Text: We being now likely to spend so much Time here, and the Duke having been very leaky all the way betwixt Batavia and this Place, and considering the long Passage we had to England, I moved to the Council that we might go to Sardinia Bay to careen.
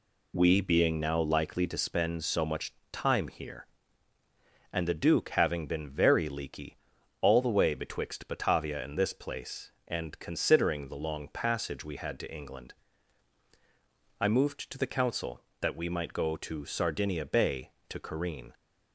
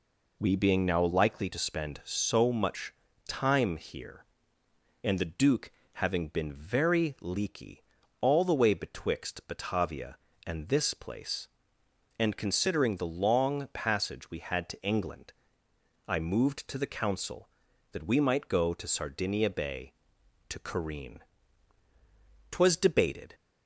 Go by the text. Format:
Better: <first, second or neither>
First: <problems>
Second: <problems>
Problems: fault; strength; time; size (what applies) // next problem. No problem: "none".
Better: first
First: pauses between "much" and "Time"; slight; at 2.7 s; 0.18 s long // pauses between "leaky" and "all"; at 6.7 s; 0.44 s long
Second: pauses between "much" and "Time"; slight; at 2.9 s; 0.36 s long // pauses between "Duke" and "having"; slight; at 5.7 s; 0.22 s long // pauses between "leaky" and "all"; at 7.8 s; 0.38 s long // goes on to say "Twas debated"; noticeable; from 22.5 s on; 0.82 s long